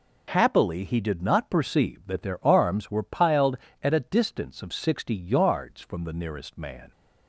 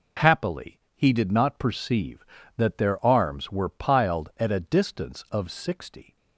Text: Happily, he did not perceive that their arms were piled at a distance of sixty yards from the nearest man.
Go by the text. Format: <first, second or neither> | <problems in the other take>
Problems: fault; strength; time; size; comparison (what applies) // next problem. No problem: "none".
first | stops before "yards from the nearest man"; at 6.1 s